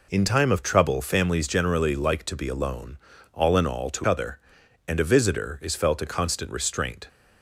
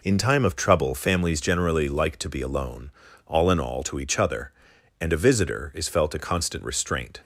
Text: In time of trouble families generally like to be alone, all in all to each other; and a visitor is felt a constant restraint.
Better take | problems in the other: second | skips "each"; at 4.0 s

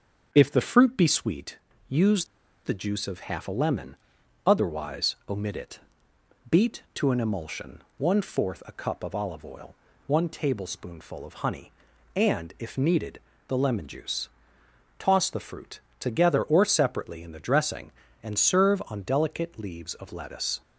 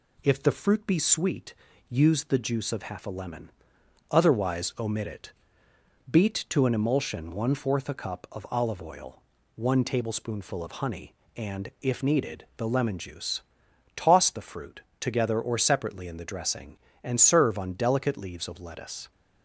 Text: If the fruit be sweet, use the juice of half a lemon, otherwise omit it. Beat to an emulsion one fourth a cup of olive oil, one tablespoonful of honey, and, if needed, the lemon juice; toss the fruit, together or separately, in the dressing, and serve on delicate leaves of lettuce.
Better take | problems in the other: second | starts louder than the rest; strong; until 1.3 s; 7 dB // pauses between "use" and "the"; at 2.2 s; 0.39 s long // pauses between "emulsion" and "one"; slight; at 7.8 s; 0.16 s long

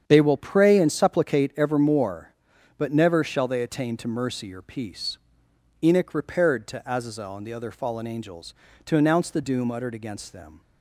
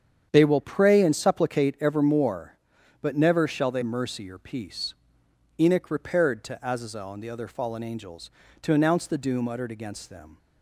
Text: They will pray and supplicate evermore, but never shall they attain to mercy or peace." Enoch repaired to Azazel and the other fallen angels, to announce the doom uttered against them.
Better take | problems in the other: first | starts louder than the rest; strong; until 1.3 s; 8.5 dB; strong in the first // skips "attain to"; at 3.8 s

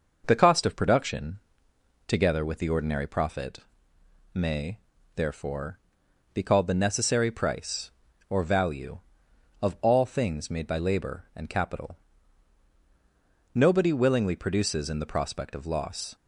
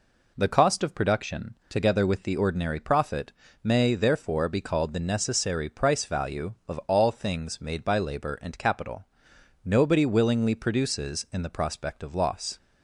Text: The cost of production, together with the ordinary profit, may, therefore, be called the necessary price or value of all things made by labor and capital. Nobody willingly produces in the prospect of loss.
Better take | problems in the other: first | skips "or"; at 6.0 s

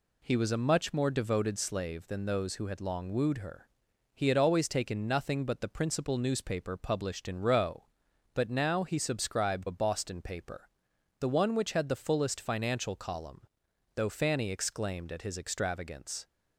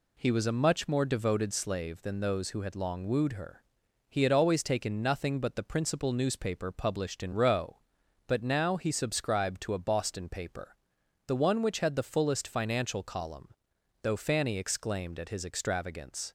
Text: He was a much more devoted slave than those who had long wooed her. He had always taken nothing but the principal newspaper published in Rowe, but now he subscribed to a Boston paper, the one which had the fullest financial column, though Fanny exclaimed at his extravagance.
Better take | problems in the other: second | skips "to"; at 9.6 s

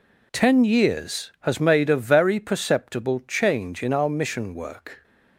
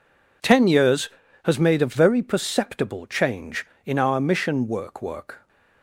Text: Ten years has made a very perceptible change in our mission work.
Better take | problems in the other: first | says "work" twice; at 5.0 s

